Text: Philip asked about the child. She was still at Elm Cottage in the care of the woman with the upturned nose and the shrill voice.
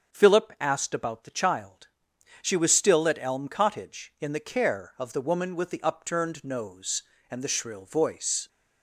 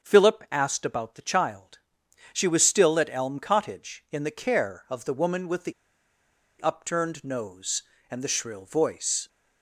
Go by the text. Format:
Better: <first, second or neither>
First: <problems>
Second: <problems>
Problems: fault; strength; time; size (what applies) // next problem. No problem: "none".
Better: first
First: starts louder than the rest; until 1.1 s; 7 dB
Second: starts louder than the rest; until 1.1 s; 7 dB // pauses between "the" and "upturned"; noticeable; at 5.7 s; 0.88 s long